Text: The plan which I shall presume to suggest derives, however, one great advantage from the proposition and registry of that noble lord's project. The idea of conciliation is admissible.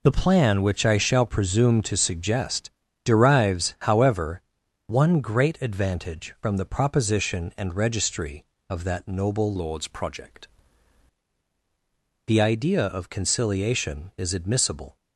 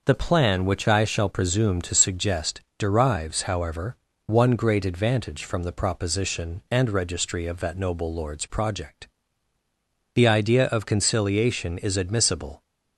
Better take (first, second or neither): second